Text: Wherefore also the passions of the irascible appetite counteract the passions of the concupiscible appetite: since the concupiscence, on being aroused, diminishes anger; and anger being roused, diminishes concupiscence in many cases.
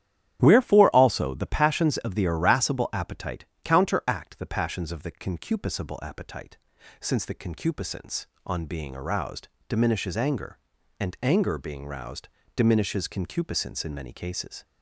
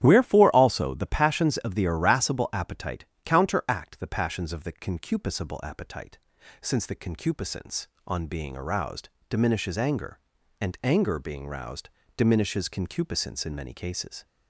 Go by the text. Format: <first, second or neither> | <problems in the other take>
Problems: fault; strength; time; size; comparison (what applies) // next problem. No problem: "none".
neither | starts louder than the rest; strong; the same in both // pauses between "appetite" and "counteract"; slight; the same in both